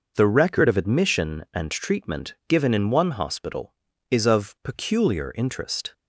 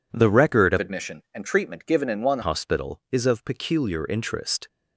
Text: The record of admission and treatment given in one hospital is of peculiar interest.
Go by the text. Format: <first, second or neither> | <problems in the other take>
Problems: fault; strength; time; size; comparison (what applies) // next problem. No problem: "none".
first | changes voice from "admission" to "one"; from 0.7 to 2.3 s; 1.6 s long